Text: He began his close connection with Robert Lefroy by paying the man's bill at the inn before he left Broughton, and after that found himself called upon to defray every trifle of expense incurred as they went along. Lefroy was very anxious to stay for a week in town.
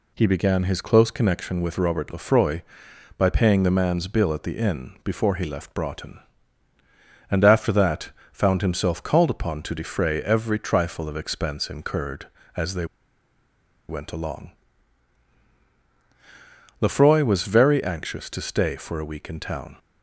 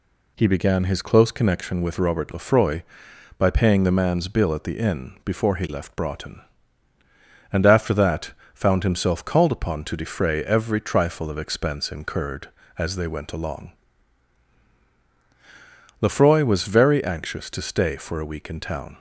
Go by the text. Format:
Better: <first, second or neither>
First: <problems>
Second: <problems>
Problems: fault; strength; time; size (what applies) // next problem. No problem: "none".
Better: second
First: pauses between "that" and "found"; slight; at 8.1 s; 0.20 s long // pauses between "they" and "went"; at 12.8 s; 1.0 s long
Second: pauses between "that" and "found"; slight; at 8.3 s; 0.20 s long